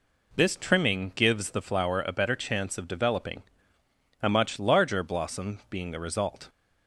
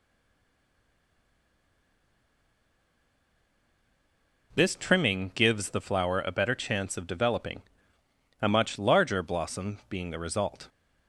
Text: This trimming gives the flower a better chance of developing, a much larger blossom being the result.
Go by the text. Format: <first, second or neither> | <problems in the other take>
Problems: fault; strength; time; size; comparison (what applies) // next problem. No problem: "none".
first | stays silent before the first word; strong; until 4.5 s; 4.5 s long